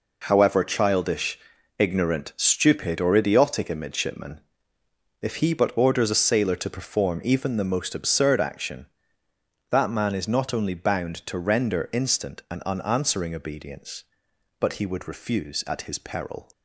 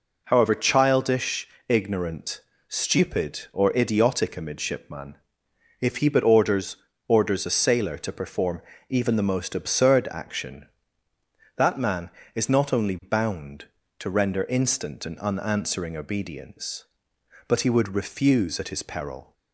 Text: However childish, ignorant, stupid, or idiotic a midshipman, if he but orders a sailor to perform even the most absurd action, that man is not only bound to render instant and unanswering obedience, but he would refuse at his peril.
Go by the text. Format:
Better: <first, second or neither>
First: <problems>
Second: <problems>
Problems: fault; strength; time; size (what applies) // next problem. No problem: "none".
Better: first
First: none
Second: says "orders" twice; at 7.0 s // pauses between "perform" and "even"; slight; at 8.6 s; 0.26 s long